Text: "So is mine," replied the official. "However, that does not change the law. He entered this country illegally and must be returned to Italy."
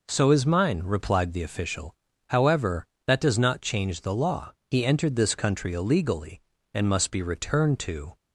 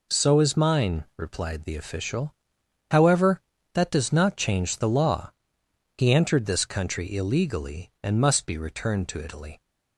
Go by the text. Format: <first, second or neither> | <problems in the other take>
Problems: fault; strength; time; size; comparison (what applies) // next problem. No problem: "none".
second | stops before "Italy"; at 8.1 s